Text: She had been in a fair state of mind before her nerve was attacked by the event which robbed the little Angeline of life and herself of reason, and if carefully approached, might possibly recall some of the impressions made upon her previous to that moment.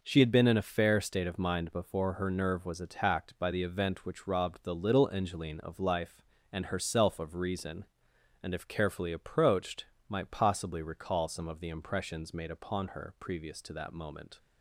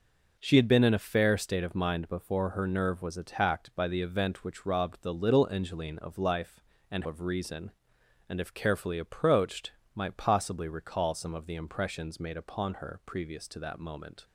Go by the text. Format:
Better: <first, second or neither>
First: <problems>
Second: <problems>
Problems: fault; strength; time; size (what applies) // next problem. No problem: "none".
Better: first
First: none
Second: skips "herself"; at 7.0 s